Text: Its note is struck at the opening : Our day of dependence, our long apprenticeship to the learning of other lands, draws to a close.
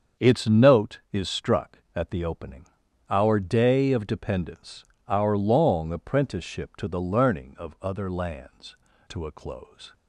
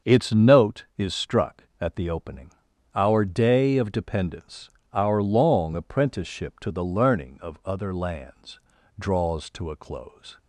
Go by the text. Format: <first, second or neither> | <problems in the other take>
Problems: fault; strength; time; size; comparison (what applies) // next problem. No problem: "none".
second | starts louder than the rest; until 1.3 s; 7 dB; also in the second // skips "draws"; at 8.9 s